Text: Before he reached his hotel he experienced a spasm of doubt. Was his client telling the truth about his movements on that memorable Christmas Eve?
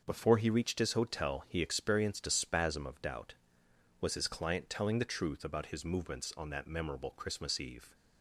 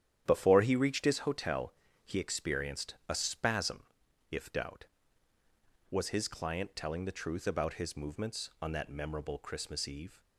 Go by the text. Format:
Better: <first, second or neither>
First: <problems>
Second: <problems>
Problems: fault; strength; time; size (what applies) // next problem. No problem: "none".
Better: first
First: starts louder than the rest; until 1.0 s; 6.5 dB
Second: starts louder than the rest; strong; until 1.2 s; 10 dB // pauses between "hotel" and "he"; slight; at 1.7 s; 0.32 s long // says "if" for "of"; at 4.2 s